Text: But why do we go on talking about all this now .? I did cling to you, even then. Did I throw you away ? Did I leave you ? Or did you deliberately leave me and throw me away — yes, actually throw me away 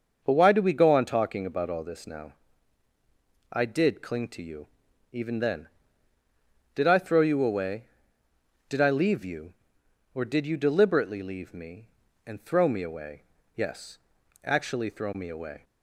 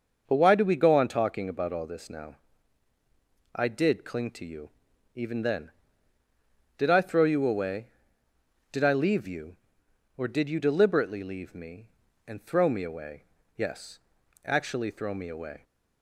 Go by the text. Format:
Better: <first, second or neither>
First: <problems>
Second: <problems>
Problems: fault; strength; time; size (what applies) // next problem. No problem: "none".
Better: neither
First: starts louder than the rest; until 1.2 s; 6 dB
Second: starts louder than the rest; until 1.2 s; 6 dB